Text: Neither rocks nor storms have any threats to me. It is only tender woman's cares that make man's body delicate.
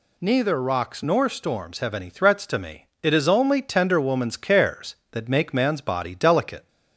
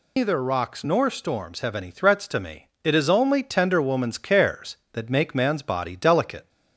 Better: first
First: none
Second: loses the start of "Neither"; at 0.1 s; 160 ms

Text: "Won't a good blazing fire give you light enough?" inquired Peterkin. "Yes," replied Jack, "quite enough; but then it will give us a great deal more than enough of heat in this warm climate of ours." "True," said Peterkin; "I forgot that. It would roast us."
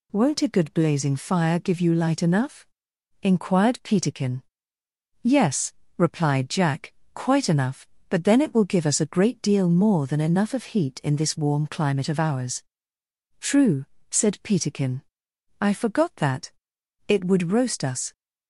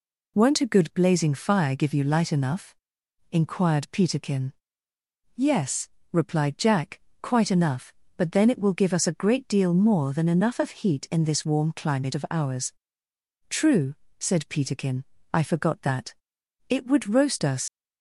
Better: first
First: none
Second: leaves "us" unfinished; at 17.6 s; 80 ms

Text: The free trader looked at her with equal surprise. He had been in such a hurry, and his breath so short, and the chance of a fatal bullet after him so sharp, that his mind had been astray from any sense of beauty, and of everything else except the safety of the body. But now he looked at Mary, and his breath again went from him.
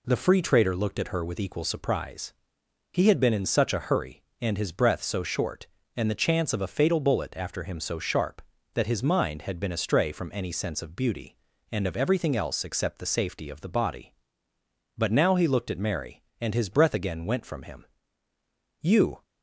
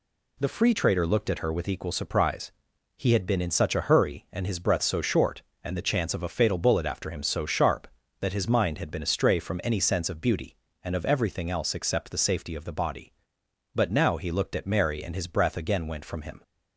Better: second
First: goes on to say "You"; slight; from 18.8 s on; 0.40 s long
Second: none

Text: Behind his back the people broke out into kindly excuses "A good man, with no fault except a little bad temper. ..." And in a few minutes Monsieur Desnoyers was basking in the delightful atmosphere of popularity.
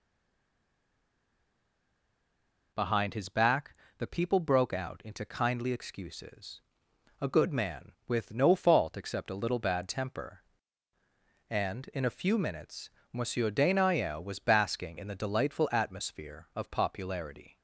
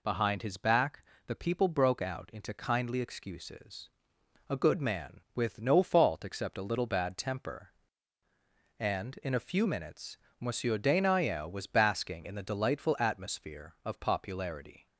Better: second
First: stays silent before the first word; strong; until 2.7 s; 2.7 s long // pauses between "back" and "the"; slight; at 3.7 s; 0.24 s long // pauses between "excuses" and "A"; noticeable; at 6.6 s; 0.60 s long // pauses between "minutes" and "Monsieur"; slight; at 12.8 s; 0.22 s long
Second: pauses between "back" and "the"; slight; at 1.0 s; 0.24 s long // pauses between "excuses" and "A"; noticeable; at 3.8 s; 0.60 s long // pauses between "minutes" and "Monsieur"; slight; at 10.1 s; 0.22 s long

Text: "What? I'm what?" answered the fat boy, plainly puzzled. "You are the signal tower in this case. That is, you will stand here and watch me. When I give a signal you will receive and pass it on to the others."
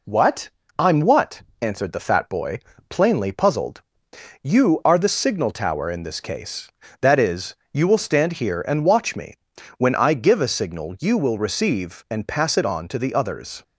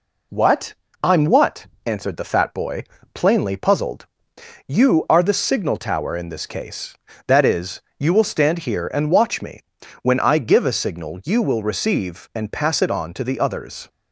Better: neither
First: none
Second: none

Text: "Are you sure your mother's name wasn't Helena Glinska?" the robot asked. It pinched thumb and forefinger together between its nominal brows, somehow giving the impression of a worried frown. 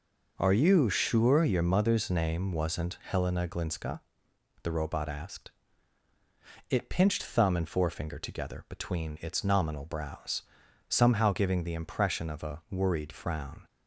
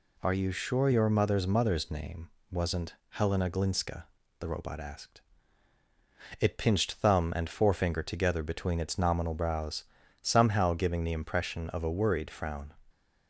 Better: first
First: none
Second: says "mother's" twice; at 1.4 s // pauses between "name" and "wasn't"; slight; at 2.3 s; 0.20 s long // pauses between "wasn't" and "Helena"; slight; at 2.9 s; 0.16 s long

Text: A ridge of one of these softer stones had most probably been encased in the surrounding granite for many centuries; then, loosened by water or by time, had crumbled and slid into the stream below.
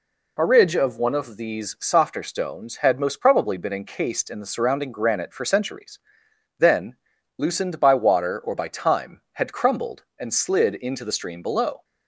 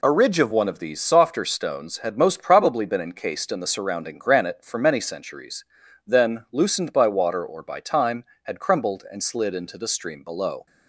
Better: second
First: skips "many"; at 5.4 s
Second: none

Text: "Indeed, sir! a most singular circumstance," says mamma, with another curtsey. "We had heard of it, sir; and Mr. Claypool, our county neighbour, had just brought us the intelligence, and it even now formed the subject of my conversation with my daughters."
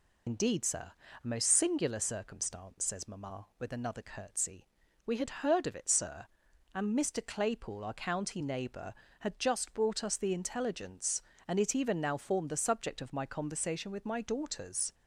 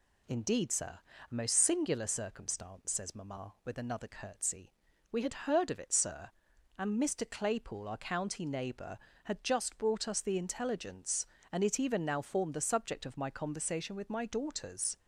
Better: second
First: loses the start of "Indeed"; at 0.2 s; 80 ms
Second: none

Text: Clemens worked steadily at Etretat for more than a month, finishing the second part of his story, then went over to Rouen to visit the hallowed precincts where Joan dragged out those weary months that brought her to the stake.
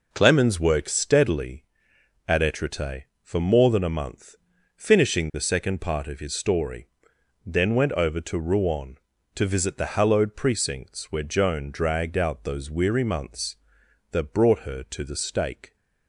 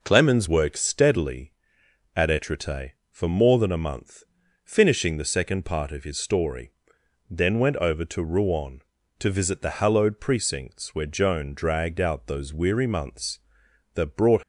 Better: first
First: none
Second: stops before "her to the stake"; at 14.4 s

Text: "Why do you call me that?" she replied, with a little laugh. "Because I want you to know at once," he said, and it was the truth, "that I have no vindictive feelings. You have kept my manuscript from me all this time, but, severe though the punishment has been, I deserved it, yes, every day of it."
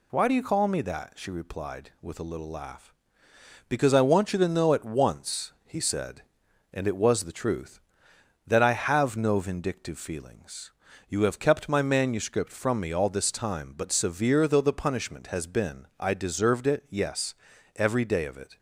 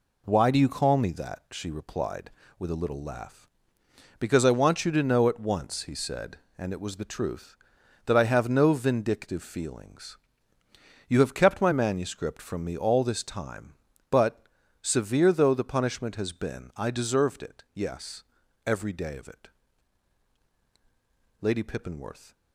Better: first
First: none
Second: goes on to say "Lady Pippinworth"; noticeable; from 21.4 s on; 0.92 s long

